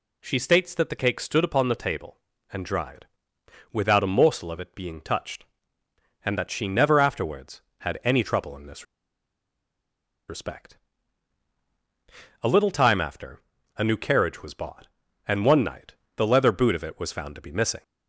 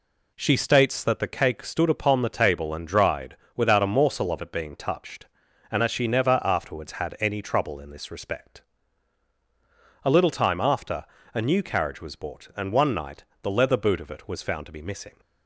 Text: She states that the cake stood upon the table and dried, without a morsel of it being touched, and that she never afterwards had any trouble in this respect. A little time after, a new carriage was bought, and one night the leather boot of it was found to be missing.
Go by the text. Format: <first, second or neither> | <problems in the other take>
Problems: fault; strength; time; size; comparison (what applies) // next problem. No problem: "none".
second | pauses between "this" and "respect"; strong; at 8.8 s; 1.4 s long // pauses between "night" and "the"; slight; at 15.9 s; 0.22 s long; slight in the second